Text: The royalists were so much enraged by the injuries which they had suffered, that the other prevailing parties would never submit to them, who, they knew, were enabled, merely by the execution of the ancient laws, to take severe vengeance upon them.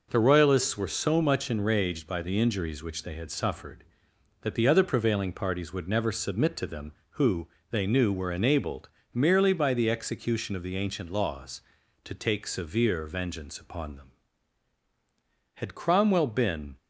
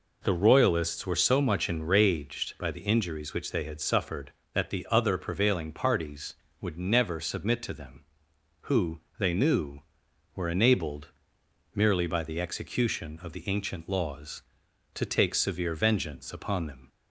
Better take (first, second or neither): second